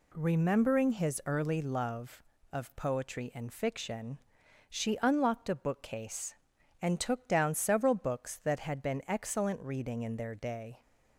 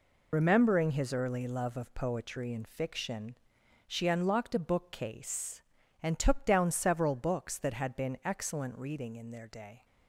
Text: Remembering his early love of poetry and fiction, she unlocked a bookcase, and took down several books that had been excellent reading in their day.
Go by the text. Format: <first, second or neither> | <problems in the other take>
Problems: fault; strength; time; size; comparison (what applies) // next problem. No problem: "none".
first | loses the start of "Remembering"; at 0.3 s; 70 ms